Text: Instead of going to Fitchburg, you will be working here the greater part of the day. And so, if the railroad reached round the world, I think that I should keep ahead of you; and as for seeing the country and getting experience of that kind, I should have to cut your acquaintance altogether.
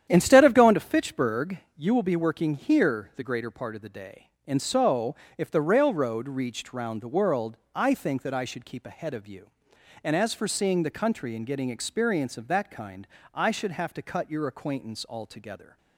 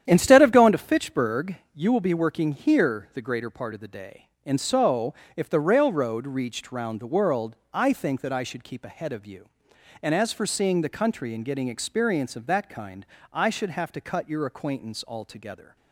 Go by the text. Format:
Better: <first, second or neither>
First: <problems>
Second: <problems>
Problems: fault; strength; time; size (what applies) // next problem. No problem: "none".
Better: neither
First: starts louder than the rest; strong; until 1.1 s; 10 dB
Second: starts louder than the rest; strong; until 1.0 s; 10 dB